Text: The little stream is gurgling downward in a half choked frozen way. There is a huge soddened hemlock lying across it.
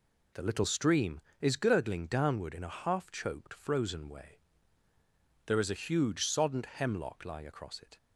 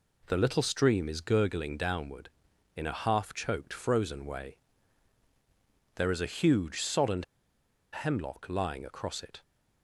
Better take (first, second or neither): first